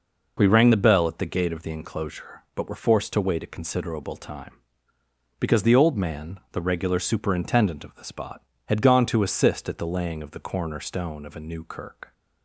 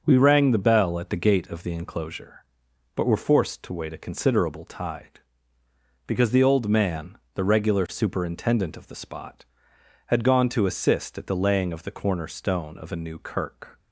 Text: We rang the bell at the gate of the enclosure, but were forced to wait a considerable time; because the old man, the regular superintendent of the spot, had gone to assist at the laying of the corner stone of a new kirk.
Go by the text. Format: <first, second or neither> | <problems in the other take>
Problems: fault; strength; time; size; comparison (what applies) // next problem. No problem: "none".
first | starts louder than the rest; until 1.0 s; 6.5 dB // says "tide" for "time"; at 4.6 s